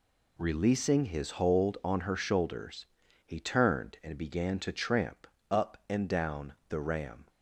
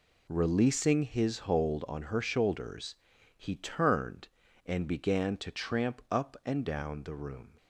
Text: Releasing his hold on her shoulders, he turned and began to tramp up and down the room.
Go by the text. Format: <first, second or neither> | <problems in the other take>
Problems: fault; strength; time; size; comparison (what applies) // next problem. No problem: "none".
second | pauses between "tramp" and "up"; slight; at 5.2 s; 0.24 s long // pauses between "down" and "the"; slight; at 6.5 s; 0.16 s long // says "ram" for "room"; at 6.7 s